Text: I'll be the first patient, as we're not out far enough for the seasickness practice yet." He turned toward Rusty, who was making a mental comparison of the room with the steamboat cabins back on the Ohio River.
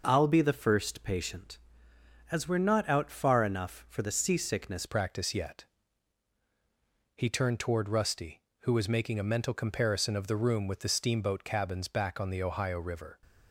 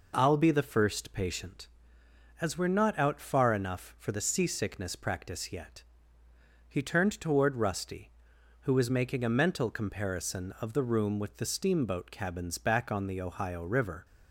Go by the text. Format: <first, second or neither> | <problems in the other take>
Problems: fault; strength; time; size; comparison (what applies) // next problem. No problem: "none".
second | changes voice at "practice"; from 4.8 s on; 8.4 s long